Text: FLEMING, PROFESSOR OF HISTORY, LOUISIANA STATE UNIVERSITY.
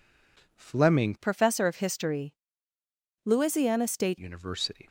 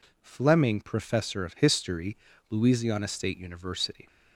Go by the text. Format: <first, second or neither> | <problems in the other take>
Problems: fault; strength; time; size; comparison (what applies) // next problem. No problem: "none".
second | changes voice from "PROFESSOR" to "STATE"; from 1.1 to 4.1 s; 3.0 s long